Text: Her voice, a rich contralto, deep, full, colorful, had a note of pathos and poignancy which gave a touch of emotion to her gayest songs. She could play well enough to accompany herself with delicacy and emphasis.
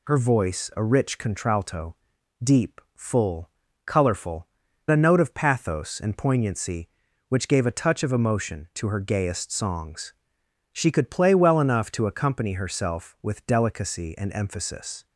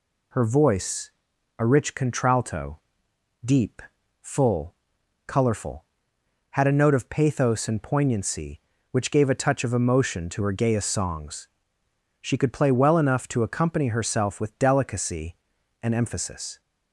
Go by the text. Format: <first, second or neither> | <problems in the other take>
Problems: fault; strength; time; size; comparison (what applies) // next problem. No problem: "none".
second | skips "had"; at 4.6 s